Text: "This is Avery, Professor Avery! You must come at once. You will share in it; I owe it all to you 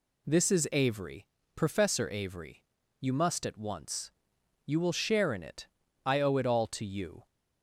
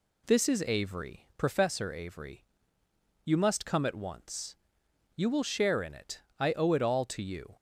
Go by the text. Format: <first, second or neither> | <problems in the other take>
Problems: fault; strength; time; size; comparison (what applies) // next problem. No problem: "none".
second | skips "come"; at 3.4 s